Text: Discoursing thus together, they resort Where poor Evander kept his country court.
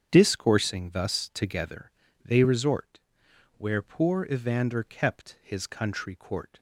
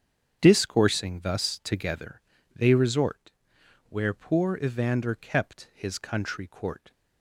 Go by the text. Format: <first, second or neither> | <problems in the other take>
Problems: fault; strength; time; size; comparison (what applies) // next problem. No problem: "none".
neither | starts louder than the rest; strong; the same in both // pauses between "resort" and "Where"; noticeable; the same in both